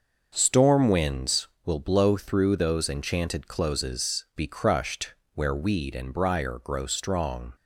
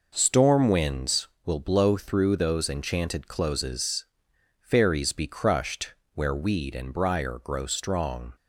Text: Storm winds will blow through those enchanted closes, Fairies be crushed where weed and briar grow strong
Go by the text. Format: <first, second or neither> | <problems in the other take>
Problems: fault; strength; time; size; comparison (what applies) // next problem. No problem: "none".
second | starts louder than the rest; until 1.3 s; 6 dB // skips "Fairies"; at 4.3 s // pauses between "crushed" and "where"; slight; at 5.1 s; 0.20 s long; slight in the second